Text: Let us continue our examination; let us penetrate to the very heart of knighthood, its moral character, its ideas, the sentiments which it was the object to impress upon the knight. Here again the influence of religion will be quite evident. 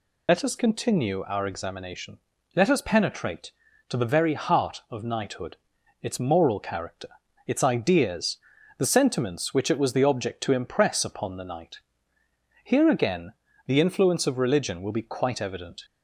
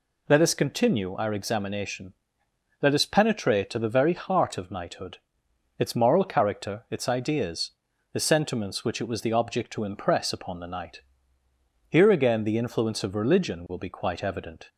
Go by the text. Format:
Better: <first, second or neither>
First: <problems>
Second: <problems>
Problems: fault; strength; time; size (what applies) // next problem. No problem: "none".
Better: second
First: loses the start of "Let"; at 0.2 s; 50 ms // pauses between "again" and "the"; slight; at 13.3 s; 0.34 s long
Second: none